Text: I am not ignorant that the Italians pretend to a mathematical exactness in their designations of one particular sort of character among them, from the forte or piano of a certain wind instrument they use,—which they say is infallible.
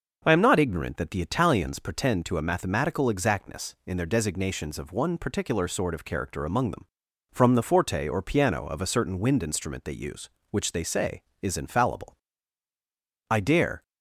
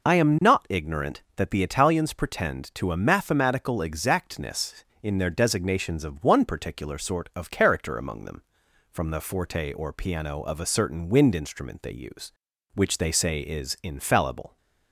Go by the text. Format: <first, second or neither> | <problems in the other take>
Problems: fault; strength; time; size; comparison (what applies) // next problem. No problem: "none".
second | goes on to say "I dare"; from 13.2 s on; 0.54 s long